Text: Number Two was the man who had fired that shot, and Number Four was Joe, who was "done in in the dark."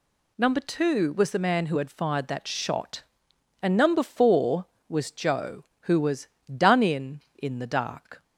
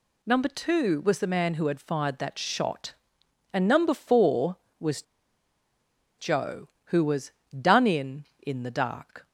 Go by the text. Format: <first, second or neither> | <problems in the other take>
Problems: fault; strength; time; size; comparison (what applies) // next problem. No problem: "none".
first | pauses between "was" and "Joe"; at 5.0 s; 1.1 s long // pauses between "was" and "done"; slight; at 7.3 s; 0.26 s long; slight in the first